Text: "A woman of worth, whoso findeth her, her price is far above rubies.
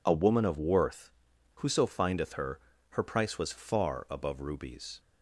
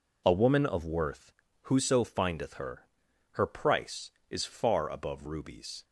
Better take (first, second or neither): second